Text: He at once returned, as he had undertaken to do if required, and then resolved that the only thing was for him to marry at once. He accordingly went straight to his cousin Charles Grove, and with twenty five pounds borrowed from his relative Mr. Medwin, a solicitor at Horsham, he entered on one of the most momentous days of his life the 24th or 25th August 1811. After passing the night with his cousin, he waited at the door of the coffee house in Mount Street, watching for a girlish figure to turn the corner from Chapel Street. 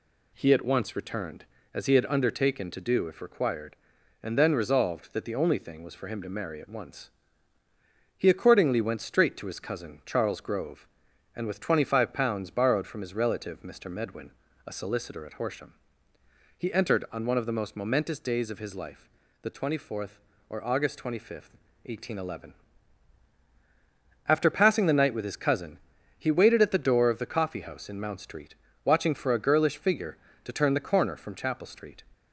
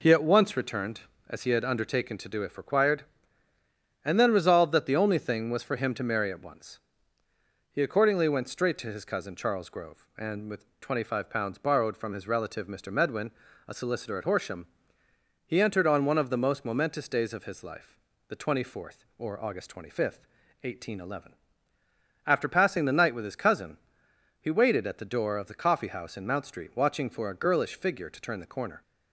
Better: first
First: pauses between "life" and "the"; slight; at 19.0 s; 0.34 s long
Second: pauses between "life" and "the"; slight; at 17.9 s; 0.32 s long // stops before "from Chapel Street"; at 28.8 s

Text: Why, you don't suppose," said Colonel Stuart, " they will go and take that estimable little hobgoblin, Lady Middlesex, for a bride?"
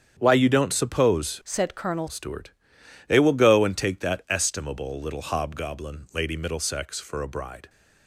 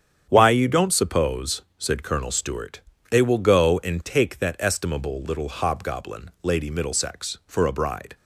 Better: second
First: starts louder than the rest; strong; until 1.2 s; 7.5 dB // changes voice from "said" to "Colonel"; from 1.4 to 2.0 s; 0.6 s long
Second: starts louder than the rest; strong; until 1.3 s; 8 dB

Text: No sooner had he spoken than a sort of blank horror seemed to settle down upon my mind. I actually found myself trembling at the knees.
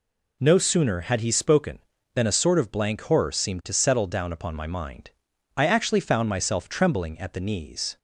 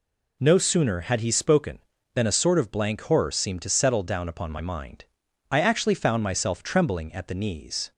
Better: neither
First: none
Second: none

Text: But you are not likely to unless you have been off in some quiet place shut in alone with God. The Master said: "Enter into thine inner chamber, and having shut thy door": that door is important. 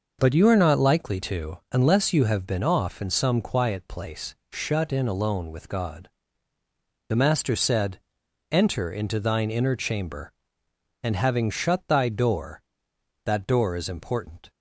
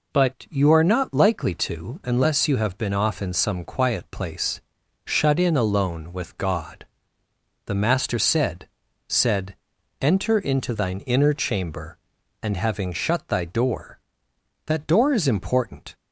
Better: first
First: pauses between "place" and "shut"; slight; at 4.3 s; 0.18 s long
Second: pauses between "place" and "shut"; noticeable; at 4.5 s; 0.46 s long // says "said" twice; at 9.0 s

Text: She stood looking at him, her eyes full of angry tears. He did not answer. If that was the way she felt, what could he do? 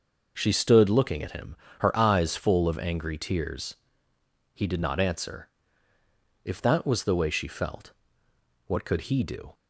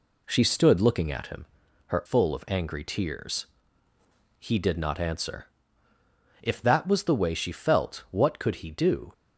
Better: first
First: none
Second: skips "eyes"; at 2.0 s

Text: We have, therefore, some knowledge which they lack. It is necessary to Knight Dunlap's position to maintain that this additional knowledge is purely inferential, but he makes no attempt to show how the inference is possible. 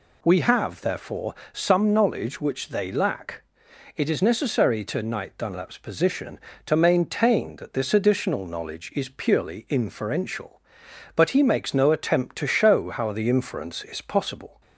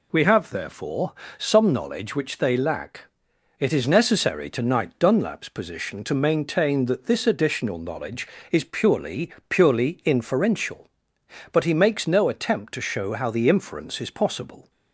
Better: first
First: none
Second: says "purely" twice; at 9.4 s

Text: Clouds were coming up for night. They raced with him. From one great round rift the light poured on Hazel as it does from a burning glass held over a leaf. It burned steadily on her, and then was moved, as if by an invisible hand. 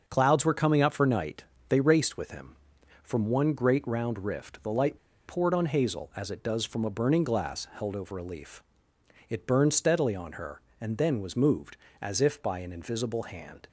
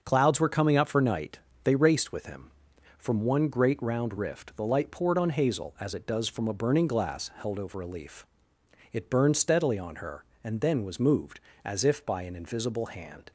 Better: second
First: starts louder than the rest; until 1.0 s; 6.5 dB // pauses between "light" and "poured"; slight; at 4.9 s; 0.31 s long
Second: starts louder than the rest; until 1.0 s; 6.5 dB

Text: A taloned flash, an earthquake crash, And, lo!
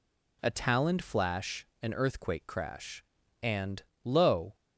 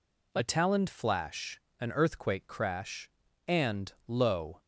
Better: neither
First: none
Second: none

